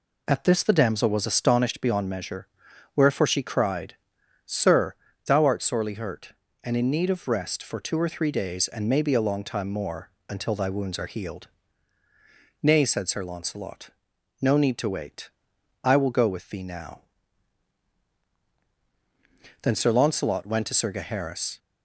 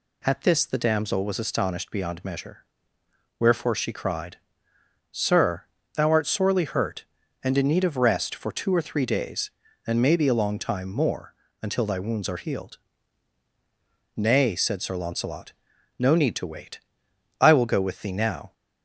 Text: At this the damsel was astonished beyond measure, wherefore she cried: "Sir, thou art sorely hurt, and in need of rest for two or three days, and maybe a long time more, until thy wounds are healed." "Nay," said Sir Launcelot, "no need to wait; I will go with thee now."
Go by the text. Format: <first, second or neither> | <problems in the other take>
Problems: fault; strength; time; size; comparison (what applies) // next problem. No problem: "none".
second | goes on to say "Then Sir Launcelot went to Sir Gaheris"; strong; from 19.6 s on; 1.9 s long